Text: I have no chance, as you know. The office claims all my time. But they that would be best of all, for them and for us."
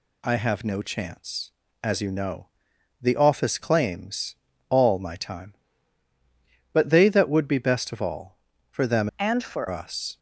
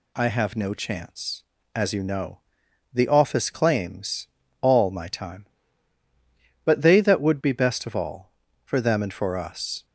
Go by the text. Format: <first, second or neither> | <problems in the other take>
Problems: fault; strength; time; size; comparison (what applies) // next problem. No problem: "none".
second | pauses between "claims" and "all"; slight; at 4.3 s; 0.34 s long; slight in the second // changes voice from "and" to "for"; from 9.1 to 9.6 s; 0.5 s long